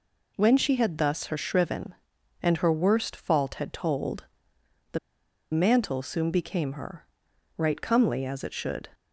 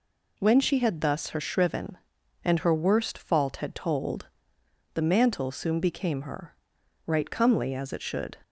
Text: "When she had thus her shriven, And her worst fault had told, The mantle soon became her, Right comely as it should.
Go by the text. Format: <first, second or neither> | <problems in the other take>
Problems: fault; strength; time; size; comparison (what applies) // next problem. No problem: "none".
second | pauses between "The" and "mantle"; noticeable; at 4.9 s; 0.53 s long